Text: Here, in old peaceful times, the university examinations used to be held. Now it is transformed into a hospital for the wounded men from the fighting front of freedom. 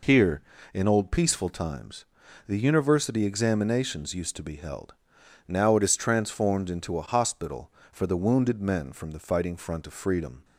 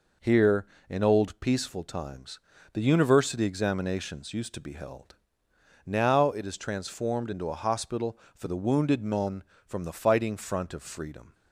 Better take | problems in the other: neither | none

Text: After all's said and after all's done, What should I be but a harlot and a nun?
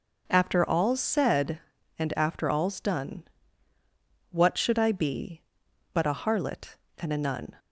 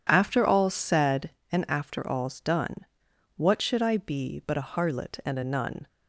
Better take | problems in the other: neither | none

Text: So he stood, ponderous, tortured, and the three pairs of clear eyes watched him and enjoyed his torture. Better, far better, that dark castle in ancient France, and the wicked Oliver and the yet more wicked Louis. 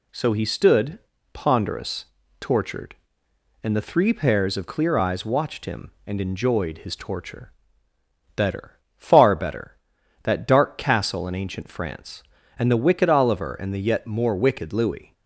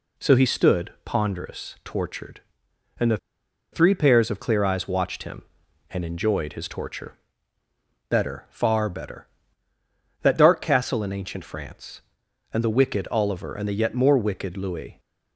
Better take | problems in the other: first | pauses between "the" and "three"; noticeable; at 3.1 s; 0.55 s long

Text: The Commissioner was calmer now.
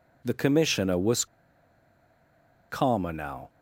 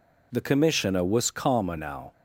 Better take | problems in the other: second | pauses between "was" and "calmer"; strong; at 1.2 s; 1.4 s long

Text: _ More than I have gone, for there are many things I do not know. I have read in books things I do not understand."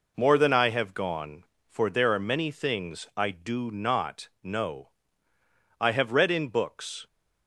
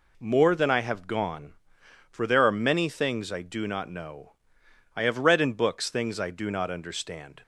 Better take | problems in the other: second | pauses between "not" and "know"; slight; at 4.2 s; 0.16 s long // stops before "things I do not understand"; at 7.0 s

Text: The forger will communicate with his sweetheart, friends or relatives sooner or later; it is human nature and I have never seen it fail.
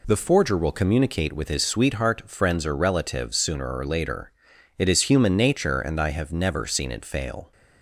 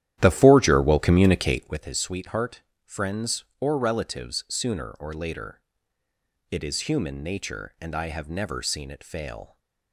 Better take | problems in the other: first | starts louder than the rest; strong; until 1.9 s; 12 dB

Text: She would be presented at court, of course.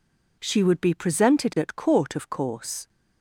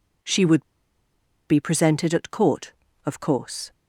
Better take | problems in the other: first | pauses between "would" and "be"; noticeable; at 0.6 s; 0.84 s long

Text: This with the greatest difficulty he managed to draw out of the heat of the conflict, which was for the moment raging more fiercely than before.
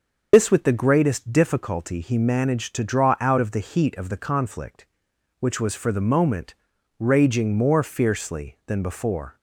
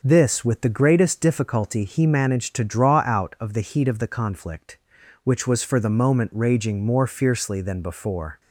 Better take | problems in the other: second | loses the start of "This"; at 0.3 s; 75 ms // starts louder than the rest; noticeable; until 1.3 s; 6 dB; also in the second // pauses between "moment" and "raging"; noticeable; at 6.5 s; 0.46 s long

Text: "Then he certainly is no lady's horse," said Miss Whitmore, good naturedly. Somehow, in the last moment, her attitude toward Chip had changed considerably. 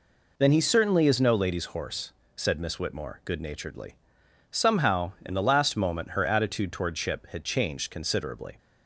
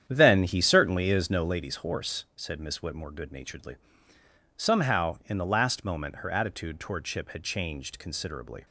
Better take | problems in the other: first | starts louder than the rest; strong; until 1.6 s; 9 dB

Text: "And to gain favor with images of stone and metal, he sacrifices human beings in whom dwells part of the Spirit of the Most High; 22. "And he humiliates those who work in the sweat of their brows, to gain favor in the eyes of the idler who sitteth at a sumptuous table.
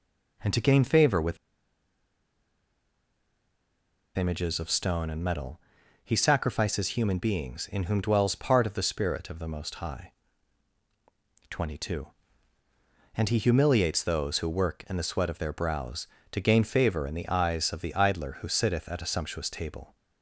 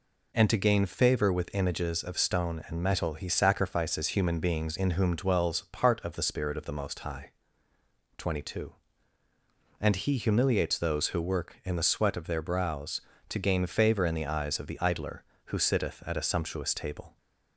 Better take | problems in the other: second | pauses between "with" and "images"; strong; at 1.3 s; 2.8 s long

